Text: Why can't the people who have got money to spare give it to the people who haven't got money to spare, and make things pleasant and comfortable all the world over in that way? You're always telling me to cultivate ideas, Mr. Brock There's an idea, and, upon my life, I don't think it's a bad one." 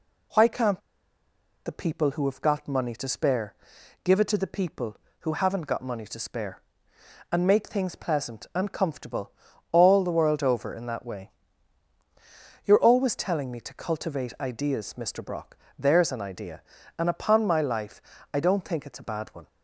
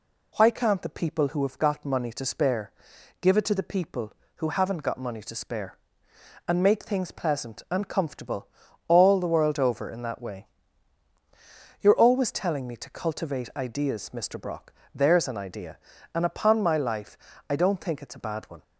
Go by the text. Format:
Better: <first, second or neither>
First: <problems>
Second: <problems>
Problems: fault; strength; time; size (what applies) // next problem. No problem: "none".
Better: second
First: pauses between "can't" and "the"; noticeable; at 0.8 s; 0.85 s long // pauses between "spare" and "give"; noticeable; at 3.5 s; 0.52 s long // pauses between "comfortable" and "all"; at 9.3 s; 0.42 s long // pauses between "Brock" and "There's"; slight; at 15.5 s; 0.20 s long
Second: pauses between "spare" and "give"; noticeable; at 2.7 s; 0.52 s long // pauses between "comfortable" and "all"; at 8.4 s; 0.42 s long // pauses between "Brock" and "There's"; slight; at 14.7 s; 0.20 s long